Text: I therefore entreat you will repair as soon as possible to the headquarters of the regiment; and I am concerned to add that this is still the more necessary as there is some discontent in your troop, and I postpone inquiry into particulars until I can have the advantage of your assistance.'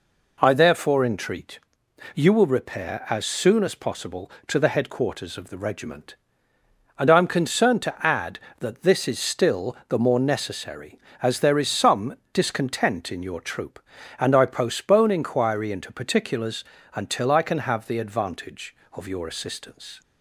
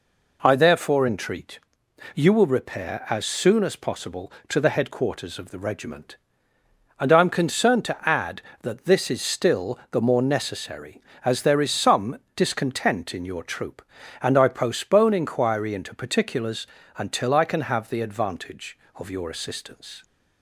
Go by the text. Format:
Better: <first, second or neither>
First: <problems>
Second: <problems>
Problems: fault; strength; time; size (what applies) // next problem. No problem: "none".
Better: neither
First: pauses between "entreat" and "you"; noticeable; at 1.5 s; 0.56 s long // pauses between "some" and "discontent"; slight; at 12.1 s; 0.18 s long // pauses between "particulars" and "until"; slight; at 16.6 s; 0.30 s long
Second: pauses between "entreat" and "you"; noticeable; at 1.5 s; 0.56 s long // pauses between "some" and "discontent"; slight; at 12.1 s; 0.18 s long // pauses between "particulars" and "until"; slight; at 16.6 s; 0.30 s long